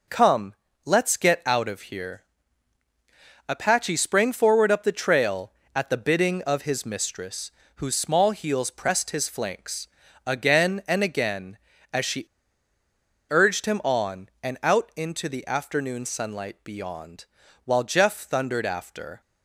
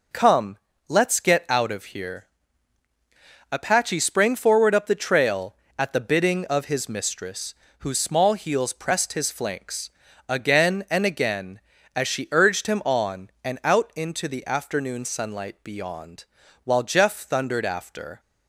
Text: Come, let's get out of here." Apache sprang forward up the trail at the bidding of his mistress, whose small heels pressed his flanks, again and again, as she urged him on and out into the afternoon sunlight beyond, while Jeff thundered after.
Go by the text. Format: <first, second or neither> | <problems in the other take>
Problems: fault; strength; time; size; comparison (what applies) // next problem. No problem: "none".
second | pauses between "she" and "urged"; at 12.2 s; 1.0 s long